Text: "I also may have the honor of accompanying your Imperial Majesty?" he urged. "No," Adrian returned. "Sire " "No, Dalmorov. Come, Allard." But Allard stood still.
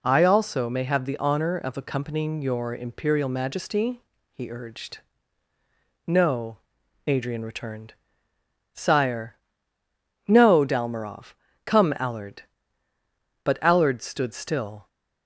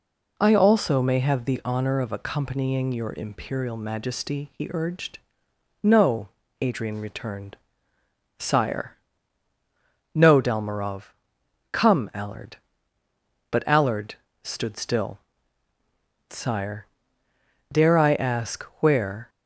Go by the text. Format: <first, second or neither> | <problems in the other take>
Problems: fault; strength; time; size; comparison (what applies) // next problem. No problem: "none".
first | pauses between "Allard" and "stood"; slight; at 14.1 s; 0.28 s long // goes on to say "Sire dare I ask where"; strong; from 16.2 s on; 3.0 s long